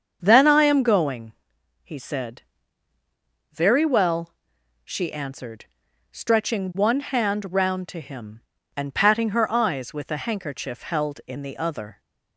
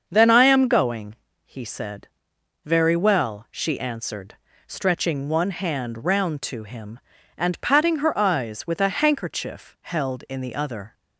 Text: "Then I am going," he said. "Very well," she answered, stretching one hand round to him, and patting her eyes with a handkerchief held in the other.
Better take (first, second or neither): neither